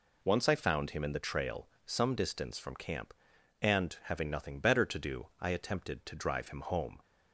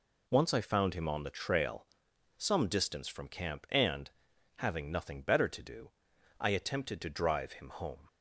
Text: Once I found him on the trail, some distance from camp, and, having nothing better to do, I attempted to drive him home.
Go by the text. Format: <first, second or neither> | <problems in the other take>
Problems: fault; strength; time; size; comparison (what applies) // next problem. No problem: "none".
second | says "in" for "on"; at 1.0 s